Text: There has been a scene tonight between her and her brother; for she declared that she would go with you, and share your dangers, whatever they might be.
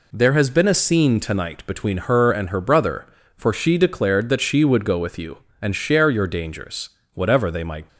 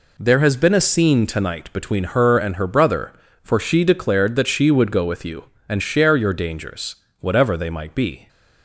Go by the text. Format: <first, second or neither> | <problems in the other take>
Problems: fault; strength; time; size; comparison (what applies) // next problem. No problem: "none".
second | stops before "be"; at 7.8 s